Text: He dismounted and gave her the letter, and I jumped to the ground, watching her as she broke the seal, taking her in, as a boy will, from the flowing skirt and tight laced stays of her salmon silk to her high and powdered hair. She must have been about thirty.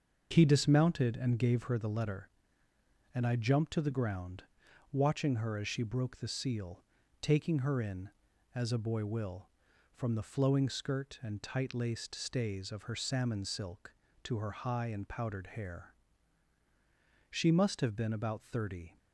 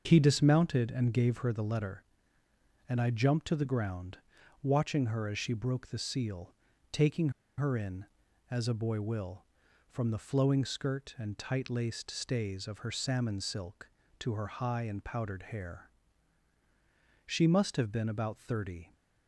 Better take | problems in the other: first | starts louder than the rest; until 1.0 s; 6.5 dB; also in the first // pauses between "taking" and "her"; slight; at 7.3 s; 0.27 s long

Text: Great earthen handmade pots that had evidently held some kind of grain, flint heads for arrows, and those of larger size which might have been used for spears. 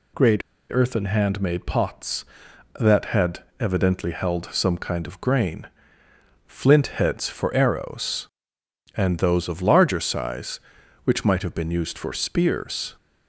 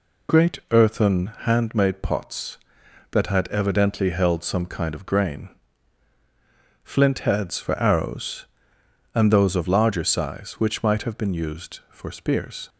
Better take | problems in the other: second | pauses between "Great" and "earthen"; slight; at 0.4 s; 0.30 s long // pauses between "had" and "evidently"; slight; at 3.4 s; 0.16 s long

